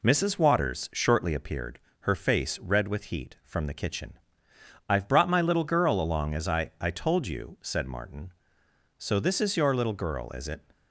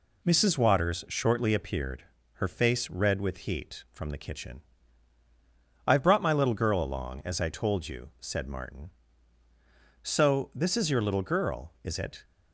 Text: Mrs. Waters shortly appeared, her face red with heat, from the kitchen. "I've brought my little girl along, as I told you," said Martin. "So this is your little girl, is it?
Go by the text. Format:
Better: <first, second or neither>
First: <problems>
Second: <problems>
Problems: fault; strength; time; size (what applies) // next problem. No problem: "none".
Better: second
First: says "I" twice; at 6.8 s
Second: none